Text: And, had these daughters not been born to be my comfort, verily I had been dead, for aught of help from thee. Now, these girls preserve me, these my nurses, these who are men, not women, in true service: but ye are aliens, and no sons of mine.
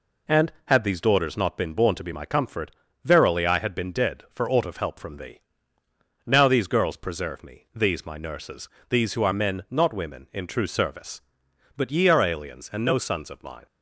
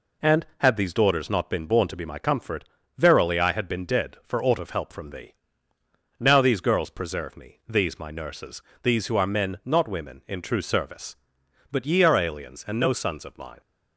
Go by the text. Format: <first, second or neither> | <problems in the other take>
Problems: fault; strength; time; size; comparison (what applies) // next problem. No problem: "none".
neither | none